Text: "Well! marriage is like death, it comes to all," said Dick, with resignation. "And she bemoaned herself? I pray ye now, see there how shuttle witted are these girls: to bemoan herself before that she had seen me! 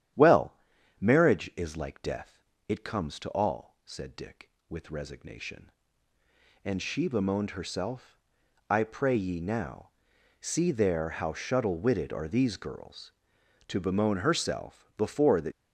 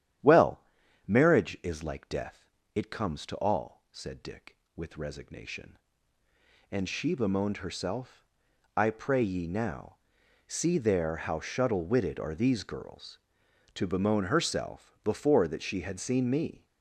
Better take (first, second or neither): second